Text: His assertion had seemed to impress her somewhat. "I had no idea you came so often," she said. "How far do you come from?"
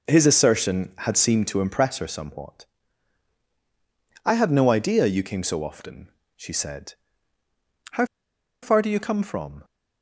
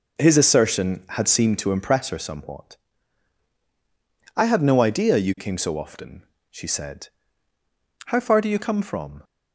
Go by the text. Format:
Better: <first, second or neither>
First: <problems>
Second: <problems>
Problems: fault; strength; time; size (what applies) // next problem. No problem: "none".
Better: second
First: pauses between "How" and "far"; noticeable; at 8.0 s; 0.57 s long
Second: none